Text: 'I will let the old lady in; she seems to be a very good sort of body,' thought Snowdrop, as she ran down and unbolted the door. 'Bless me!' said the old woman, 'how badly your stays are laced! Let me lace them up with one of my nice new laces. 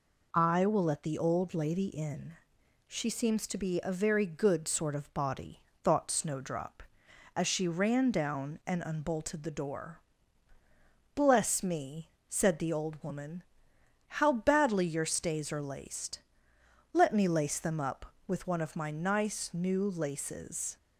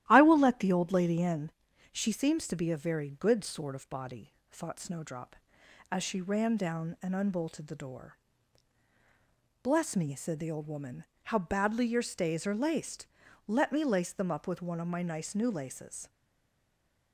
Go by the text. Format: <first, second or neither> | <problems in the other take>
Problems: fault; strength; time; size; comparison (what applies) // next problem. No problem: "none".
first | starts louder than the rest; strong; until 1.1 s; 13.5 dB // stays silent after the last word; from 16.0 s on; 1.1 s long